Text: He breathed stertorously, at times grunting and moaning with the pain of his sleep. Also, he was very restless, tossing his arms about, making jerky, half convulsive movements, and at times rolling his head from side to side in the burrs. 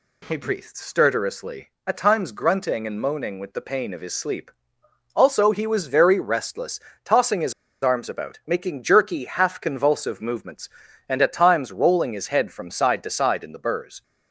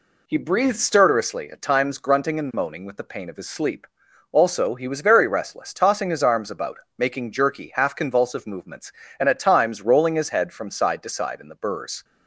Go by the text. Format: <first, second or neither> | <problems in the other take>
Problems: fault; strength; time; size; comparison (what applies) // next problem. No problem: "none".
second | pauses between "his" and "arms"; slight; at 7.5 s; 0.29 s long